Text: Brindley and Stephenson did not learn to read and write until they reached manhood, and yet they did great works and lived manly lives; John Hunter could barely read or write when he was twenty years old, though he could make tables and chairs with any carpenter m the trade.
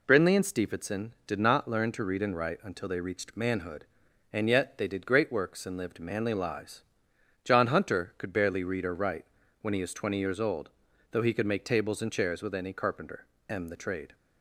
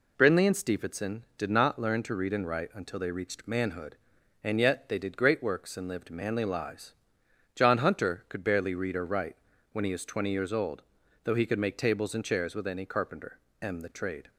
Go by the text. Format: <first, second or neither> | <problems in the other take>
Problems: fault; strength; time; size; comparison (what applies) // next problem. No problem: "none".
neither | pauses between "write" and "when"; the same in both // pauses between "carpenter" and "m"; slight; the same in both